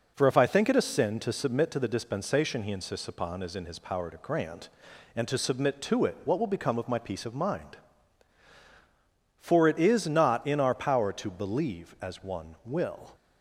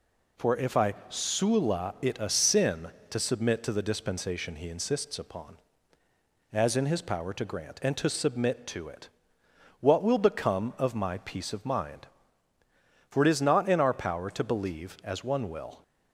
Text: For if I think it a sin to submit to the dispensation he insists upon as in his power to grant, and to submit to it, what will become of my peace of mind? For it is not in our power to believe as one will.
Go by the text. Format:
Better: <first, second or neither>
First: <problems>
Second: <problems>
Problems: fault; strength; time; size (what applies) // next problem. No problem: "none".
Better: first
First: none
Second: says "sula" for "think"; at 1.0 s